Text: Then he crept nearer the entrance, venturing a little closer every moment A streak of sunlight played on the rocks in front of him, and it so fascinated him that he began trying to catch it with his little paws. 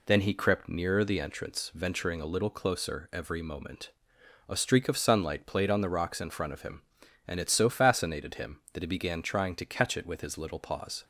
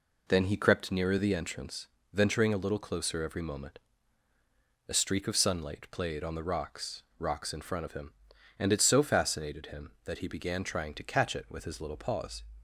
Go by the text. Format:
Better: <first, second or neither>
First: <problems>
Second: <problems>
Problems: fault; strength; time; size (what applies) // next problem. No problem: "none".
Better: first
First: pauses between "moment" and "A"; noticeable; at 3.9 s; 0.58 s long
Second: pauses between "moment" and "A"; at 3.7 s; 1.1 s long // says "rocks" twice; at 7.1 s